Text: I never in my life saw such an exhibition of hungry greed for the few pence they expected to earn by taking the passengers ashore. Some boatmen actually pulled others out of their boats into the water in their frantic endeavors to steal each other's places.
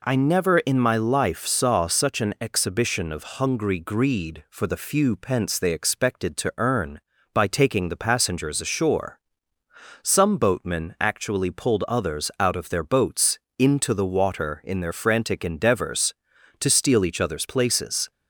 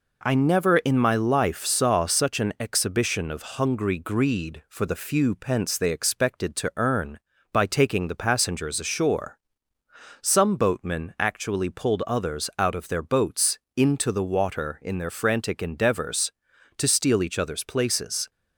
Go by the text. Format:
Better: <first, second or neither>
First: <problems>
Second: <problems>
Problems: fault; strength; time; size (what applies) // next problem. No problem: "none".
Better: first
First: pauses between "boats" and "into"; slight; at 13.3 s; 0.22 s long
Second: gets quieter; slight; throughout; 3.5 dB // pauses between "boats" and "into"; slight; at 13.5 s; 0.20 s long